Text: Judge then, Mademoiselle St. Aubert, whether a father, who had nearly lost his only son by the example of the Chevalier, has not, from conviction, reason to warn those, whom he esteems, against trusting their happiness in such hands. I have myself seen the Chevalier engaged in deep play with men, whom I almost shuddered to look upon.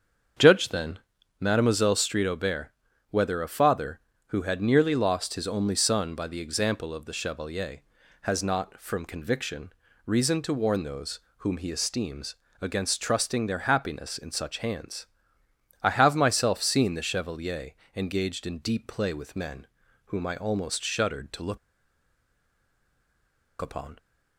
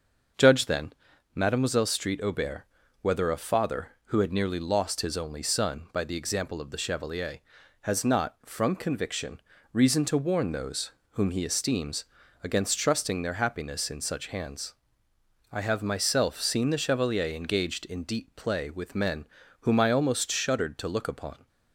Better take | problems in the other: second | starts louder than the rest; strong; until 1.7 s; 7 dB; also in the second // pauses between "Chevalier" and "engaged"; slight; at 17.7 s; 0.24 s long // pauses between "look" and "upon"; strong; at 21.5 s; 2.0 s long

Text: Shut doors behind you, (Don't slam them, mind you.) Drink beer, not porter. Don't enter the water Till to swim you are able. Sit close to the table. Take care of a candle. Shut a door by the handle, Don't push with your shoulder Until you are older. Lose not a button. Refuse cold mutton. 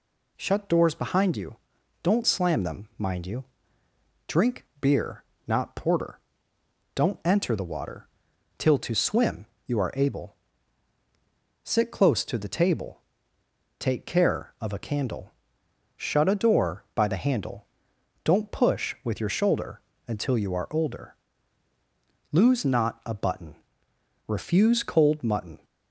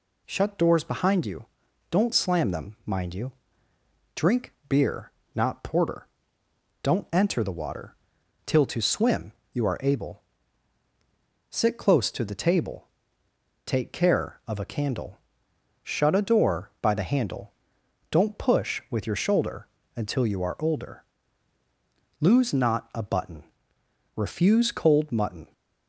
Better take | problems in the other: neither | pauses between "water" and "Till"; noticeable; the same in both // pauses between "swim" and "you"; slight; the same in both // pauses between "shoulder" and "Until"; slight; the same in both

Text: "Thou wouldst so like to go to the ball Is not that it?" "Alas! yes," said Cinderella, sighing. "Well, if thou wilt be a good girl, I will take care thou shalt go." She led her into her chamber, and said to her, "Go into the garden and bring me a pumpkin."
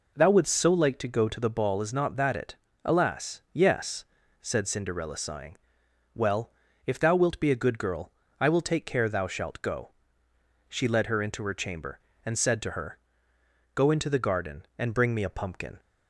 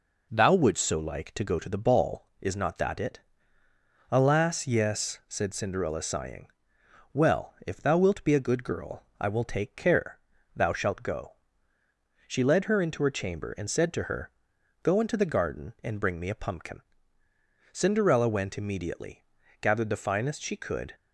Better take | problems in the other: first | pauses between "care" and "thou"; slight; at 10.1 s; 0.36 s long // goes on to say "Cinderella went immediately gathered the finest she could"; strong; from 17.7 s on; 3.2 s long

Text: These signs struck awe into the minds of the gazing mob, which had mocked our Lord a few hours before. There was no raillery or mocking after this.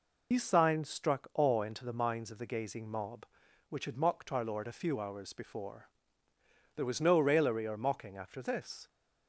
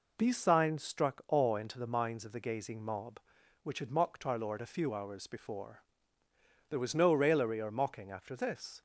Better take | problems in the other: second | loses the start of "These"; at 0.3 s; 70 ms

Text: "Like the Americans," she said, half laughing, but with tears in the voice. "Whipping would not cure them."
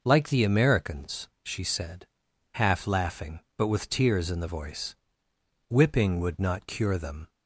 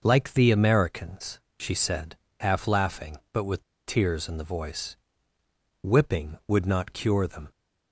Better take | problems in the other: first | pauses between "with" and "tears"; slight; at 3.6 s; 0.23 s long

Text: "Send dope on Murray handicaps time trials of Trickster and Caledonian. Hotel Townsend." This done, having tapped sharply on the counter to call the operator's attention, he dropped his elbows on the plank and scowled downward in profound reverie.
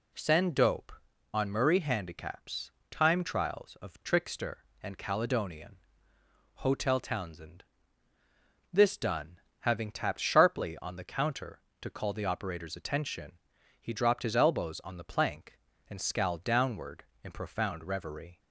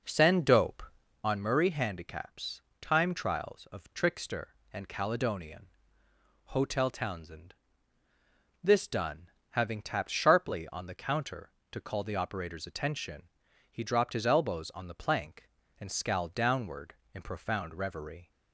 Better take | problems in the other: first | starts louder than the rest; noticeable; until 1.4 s; 5 dB // pauses between "handicaps" and "time"; slight; at 2.6 s; 0.20 s long; slight in the first

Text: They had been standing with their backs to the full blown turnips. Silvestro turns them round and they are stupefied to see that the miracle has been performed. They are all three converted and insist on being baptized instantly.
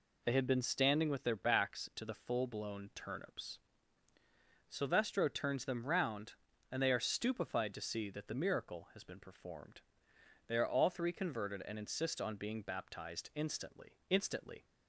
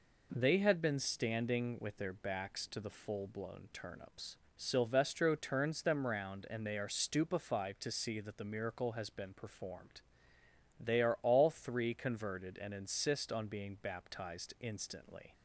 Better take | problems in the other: second | says "instantly" twice; at 14.0 s

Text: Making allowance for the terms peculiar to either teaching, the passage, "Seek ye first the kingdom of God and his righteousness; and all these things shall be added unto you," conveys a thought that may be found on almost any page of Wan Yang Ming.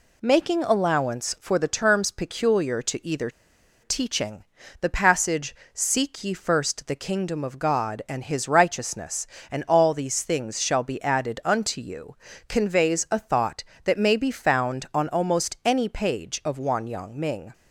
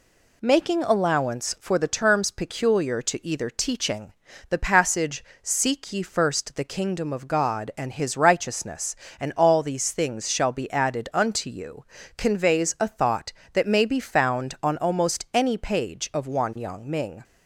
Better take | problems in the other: second | pauses between "either" and "teaching"; noticeable; at 3.2 s; 0.53 s long

